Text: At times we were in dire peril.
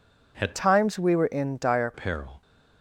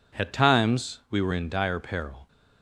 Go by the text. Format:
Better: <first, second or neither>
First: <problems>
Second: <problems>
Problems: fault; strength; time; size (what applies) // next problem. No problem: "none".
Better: second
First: changes voice from "times" to "dire"; from 0.5 to 1.9 s; 1.4 s long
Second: none